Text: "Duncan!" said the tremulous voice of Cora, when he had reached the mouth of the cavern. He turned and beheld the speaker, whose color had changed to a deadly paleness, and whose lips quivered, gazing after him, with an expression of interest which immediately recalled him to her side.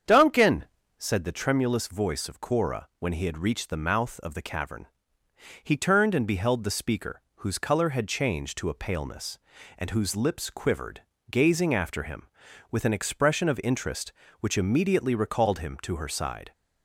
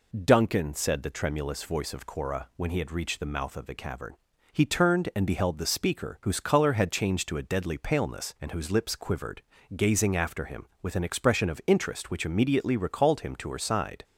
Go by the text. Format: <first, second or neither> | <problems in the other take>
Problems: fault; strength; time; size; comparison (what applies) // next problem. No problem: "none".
second | starts louder than the rest; strong; until 1.4 s; 7.5 dB // skips "deadly"; at 8.7 s